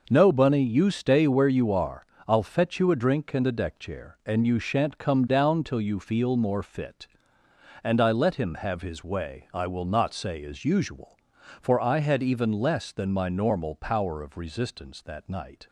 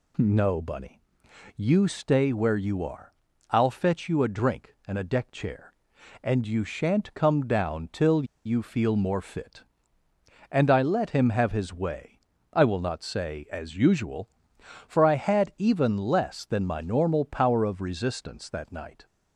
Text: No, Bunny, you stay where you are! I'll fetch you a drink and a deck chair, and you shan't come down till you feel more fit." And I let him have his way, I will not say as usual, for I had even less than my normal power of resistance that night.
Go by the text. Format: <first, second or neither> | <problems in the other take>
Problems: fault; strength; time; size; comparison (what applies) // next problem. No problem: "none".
first | pauses between "till" and "you"; slight; at 8.2 s; 0.20 s long